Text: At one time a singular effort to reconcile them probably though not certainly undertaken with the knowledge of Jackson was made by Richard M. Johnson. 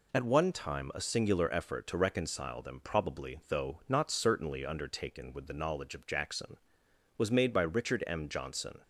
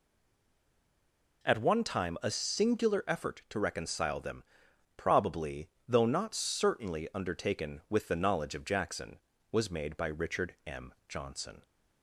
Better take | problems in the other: first | stays silent before the first word; noticeable; until 1.4 s; 1.4 s long // pauses between "them" and "probably"; noticeable; at 4.4 s; 0.52 s long // pauses between "probably" and "though"; slight; at 5.6 s; 0.18 s long

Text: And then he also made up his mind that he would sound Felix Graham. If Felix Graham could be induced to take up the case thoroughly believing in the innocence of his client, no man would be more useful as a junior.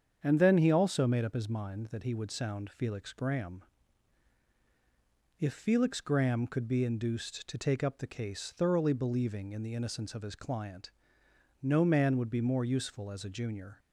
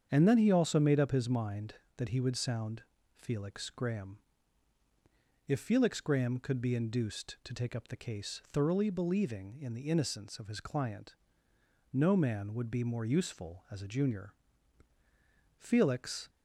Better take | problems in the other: first | starts louder than the rest; strong; until 1.1 s; 7.5 dB; strong in the first // pauses between "sound" and "Felix"; slight; at 2.8 s; 0.32 s long // goes on to say "Felix"; noticeable; from 15.5 s on; 0.72 s long

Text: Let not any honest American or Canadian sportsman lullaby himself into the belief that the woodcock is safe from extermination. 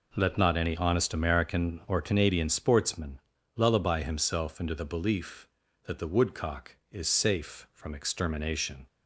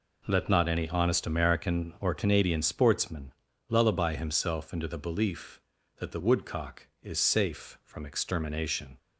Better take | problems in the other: neither | pauses between "sportsman" and "lullaby"; slight; the same in both

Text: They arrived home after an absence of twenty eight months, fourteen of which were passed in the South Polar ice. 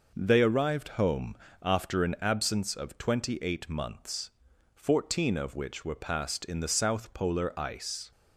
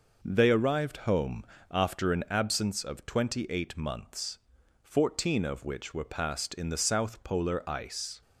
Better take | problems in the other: neither | pauses between "home" and "after"; slight; the same in both

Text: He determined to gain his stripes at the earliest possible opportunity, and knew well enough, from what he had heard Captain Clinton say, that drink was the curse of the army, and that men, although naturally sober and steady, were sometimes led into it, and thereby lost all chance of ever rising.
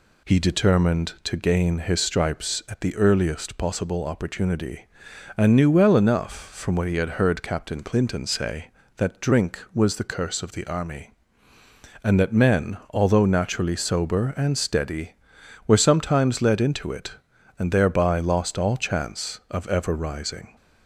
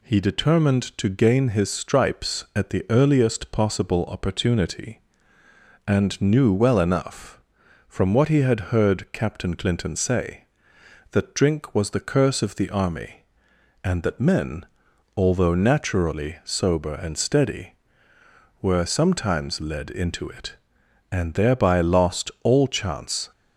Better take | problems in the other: first | stops before "of ever rising"; at 23.3 s

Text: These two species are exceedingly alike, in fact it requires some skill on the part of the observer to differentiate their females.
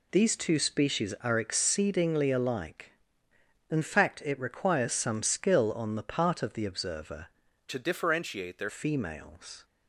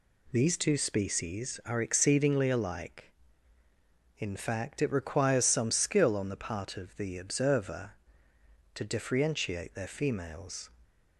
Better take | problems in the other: second | changes voice from "to" to "their"; from 7.6 to 8.6 s; 1.0 s long

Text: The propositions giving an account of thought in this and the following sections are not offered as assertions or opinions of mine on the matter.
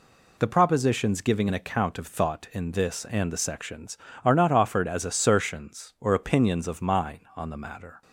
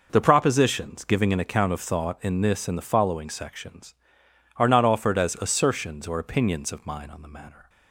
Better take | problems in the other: second | skips "following"; at 3.3 s

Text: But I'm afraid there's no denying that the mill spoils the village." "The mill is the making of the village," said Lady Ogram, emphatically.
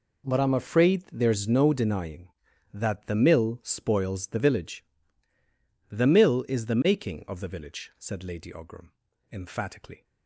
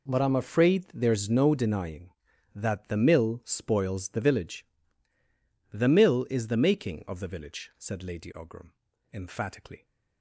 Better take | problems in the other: neither | none

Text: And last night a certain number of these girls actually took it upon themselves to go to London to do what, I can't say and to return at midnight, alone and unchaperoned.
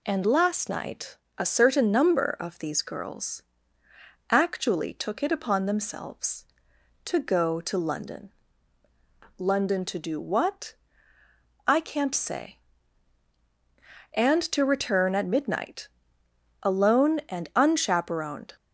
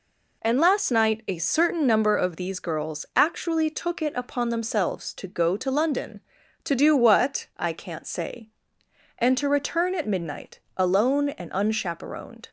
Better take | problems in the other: second | pauses between "night" and "a"; slight; at 1.1 s; 0.22 s long // pauses between "girls" and "actually"; noticeable; at 3.4 s; 0.88 s long // says "London" twice; at 9.3 s

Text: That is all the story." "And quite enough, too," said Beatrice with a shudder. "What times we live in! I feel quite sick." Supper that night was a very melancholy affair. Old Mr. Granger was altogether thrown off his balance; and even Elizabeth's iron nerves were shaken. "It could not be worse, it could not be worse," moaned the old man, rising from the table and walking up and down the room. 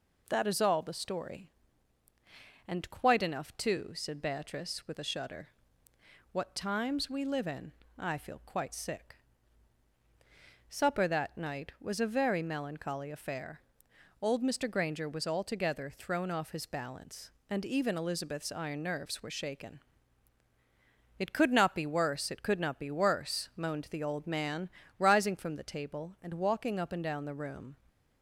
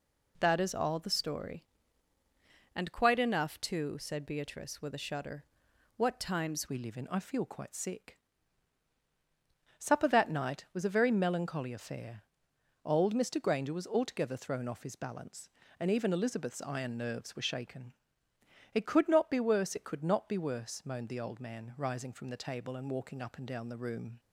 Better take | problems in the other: first | changes voice at "we"; from 6.6 s on; 17.5 s long

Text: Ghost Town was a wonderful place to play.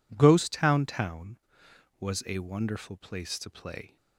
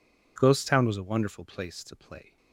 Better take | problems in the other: second | says "Town" twice; at 0.8 s

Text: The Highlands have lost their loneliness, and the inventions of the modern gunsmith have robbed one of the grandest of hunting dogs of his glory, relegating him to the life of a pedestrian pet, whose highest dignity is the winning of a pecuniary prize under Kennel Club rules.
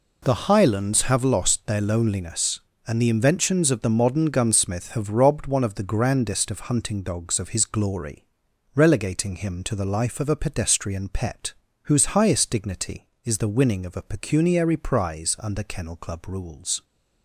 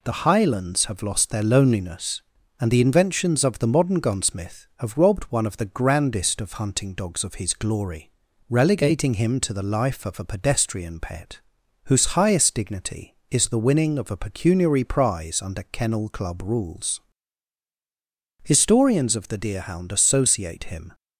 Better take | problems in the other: first | goes on to say "Historians of the Deerhound associate him"; strong; from 18.4 s on; 2.5 s long

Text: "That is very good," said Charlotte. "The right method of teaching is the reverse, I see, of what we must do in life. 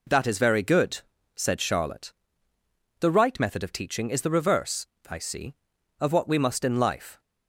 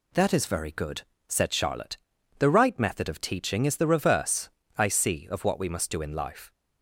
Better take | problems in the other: second | skips "do"; at 6.6 s

